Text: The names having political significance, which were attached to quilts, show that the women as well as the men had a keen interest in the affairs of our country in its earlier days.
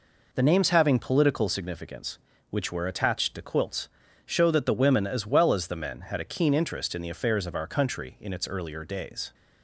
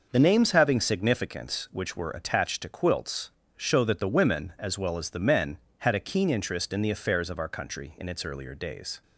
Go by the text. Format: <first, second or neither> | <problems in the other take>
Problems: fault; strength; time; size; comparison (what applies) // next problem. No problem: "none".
first | skips "political"; at 0.7 s